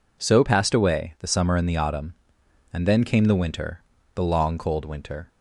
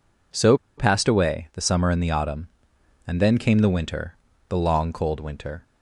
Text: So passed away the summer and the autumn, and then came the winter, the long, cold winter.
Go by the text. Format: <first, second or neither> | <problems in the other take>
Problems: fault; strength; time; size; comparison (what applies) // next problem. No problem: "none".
first | pauses between "So" and "passed"; slight; at 0.5 s; 0.22 s long